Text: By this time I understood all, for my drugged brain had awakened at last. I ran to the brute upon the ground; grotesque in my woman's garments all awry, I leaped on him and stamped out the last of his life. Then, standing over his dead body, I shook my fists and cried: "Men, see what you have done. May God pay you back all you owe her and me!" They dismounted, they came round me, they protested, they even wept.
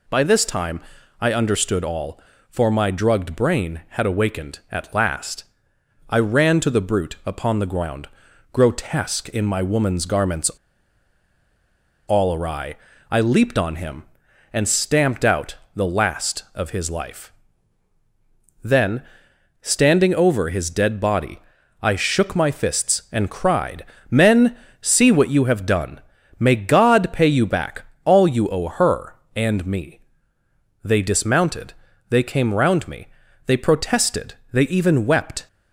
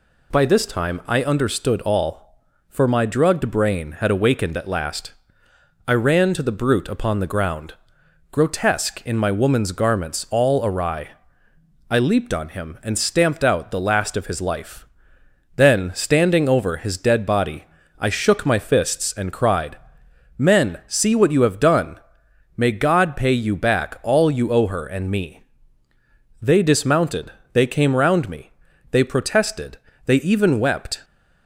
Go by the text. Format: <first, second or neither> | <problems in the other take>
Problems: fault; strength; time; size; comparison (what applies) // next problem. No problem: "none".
second | pauses between "time" and "I"; at 0.7 s; 0.40 s long // pauses between "garments" and "all"; strong; at 10.4 s; 1.5 s long // pauses between "out" and "the"; slight; at 15.5 s; 0.20 s long // pauses between "back" and "all"; slight; at 27.8 s; 0.20 s long